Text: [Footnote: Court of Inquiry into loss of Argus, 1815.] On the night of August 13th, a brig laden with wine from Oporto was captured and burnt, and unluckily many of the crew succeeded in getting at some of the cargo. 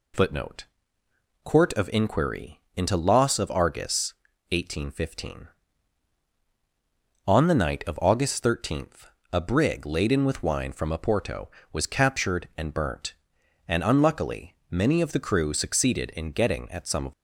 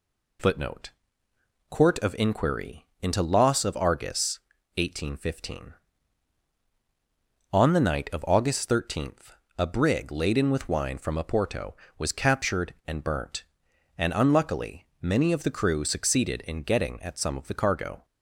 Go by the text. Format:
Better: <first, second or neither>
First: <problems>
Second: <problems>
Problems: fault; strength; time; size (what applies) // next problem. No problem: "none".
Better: second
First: pauses between "Inquiry" and "into"; slight; at 2.6 s; 0.16 s long // pauses between "unluckily" and "many"; slight; at 14.5 s; 0.16 s long // stops before "the cargo"; at 17.1 s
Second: pauses between "Inquiry" and "into"; slight; at 2.8 s; 0.16 s long // pauses between "unluckily" and "many"; slight; at 14.8 s; 0.16 s long